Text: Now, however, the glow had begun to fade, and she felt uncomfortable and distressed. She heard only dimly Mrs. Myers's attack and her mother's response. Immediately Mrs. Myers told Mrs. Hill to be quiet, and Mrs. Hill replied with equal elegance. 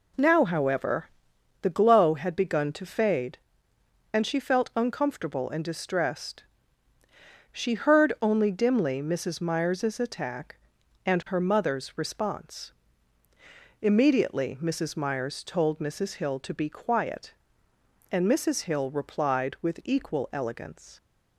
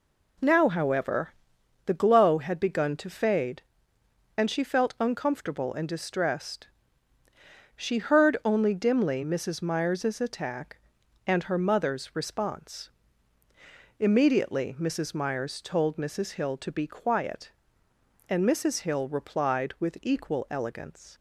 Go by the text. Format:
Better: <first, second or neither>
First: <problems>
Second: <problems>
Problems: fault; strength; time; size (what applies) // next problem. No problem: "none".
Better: neither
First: none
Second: none